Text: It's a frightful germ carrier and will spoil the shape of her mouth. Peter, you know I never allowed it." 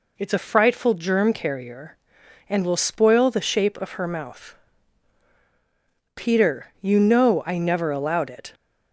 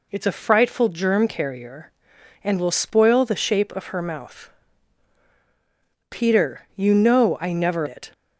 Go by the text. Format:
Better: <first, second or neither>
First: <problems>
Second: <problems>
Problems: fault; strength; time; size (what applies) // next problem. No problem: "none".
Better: first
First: none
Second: skips "allowed"; at 7.8 s